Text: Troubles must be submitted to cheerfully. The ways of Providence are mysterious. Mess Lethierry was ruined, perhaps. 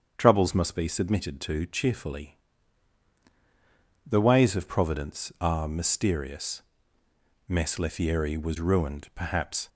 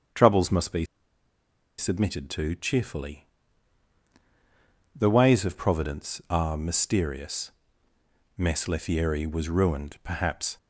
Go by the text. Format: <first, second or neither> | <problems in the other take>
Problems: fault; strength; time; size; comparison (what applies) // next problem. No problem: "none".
first | starts louder than the rest; strong; until 2.0 s; 7.5 dB; strong in the first // pauses between "be" and "submitted"; noticeable; at 0.8 s; 0.93 s long